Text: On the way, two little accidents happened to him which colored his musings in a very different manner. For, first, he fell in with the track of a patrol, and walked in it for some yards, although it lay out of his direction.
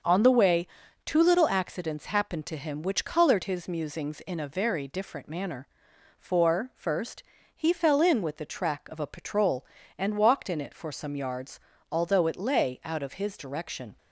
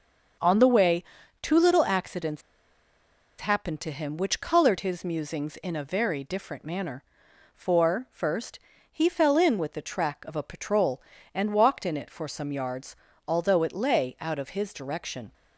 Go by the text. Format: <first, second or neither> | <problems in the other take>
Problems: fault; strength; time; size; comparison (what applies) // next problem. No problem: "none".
first | starts louder than the rest; until 1.8 s; 7 dB; also in the first // pauses between "accidents" and "happened"; at 2.4 s; 0.99 s long